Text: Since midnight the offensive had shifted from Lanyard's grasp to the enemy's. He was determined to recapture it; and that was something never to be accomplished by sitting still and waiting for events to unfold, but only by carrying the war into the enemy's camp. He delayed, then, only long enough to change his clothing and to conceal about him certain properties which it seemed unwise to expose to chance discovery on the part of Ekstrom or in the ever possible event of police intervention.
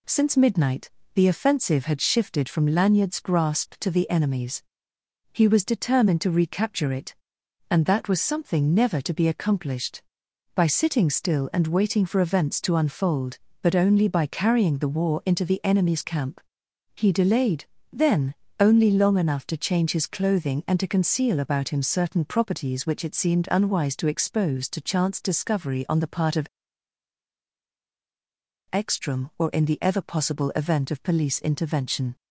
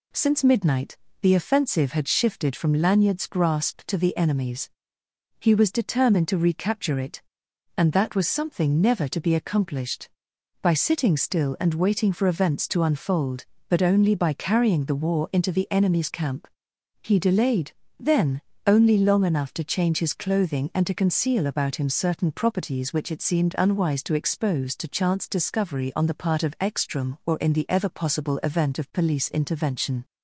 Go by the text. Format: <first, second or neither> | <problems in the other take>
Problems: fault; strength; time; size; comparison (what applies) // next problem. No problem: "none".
second | pauses between "midnight" and "the"; slight; at 0.8 s; 0.24 s long; slight in the second // pauses between "of" and "Ekstrom"; strong; at 26.4 s; 2.2 s long